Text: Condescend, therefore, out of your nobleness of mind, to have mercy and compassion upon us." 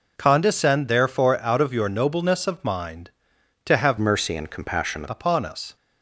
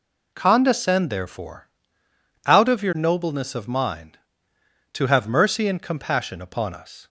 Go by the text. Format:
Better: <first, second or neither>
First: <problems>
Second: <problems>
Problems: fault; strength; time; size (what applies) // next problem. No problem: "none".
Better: second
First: changes voice from "mercy" to "compassion"; from 3.9 to 5.0 s; 1.1 s long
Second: none